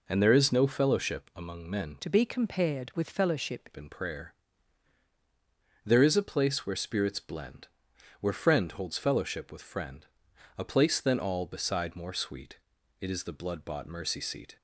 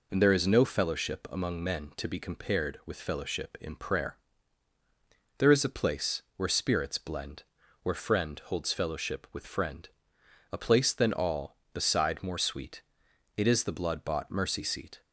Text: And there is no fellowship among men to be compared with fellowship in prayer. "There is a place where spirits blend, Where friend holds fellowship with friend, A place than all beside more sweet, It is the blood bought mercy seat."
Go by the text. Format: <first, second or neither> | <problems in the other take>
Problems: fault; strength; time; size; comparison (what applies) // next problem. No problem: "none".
second | changes voice from "to" to "fellowship"; from 1.9 to 3.6 s; 1.7 s long